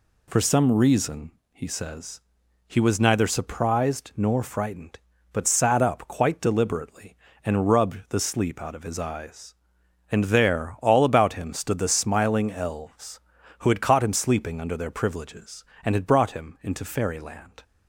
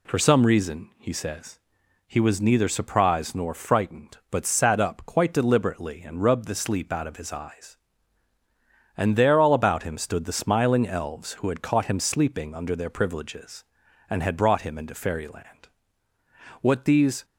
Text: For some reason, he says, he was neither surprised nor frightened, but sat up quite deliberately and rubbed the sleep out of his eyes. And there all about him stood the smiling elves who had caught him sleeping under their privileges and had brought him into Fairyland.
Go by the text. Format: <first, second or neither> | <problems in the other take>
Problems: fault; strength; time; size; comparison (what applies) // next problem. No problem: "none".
first | goes on to say "What these"; noticeable; from 16.6 s on; 0.64 s long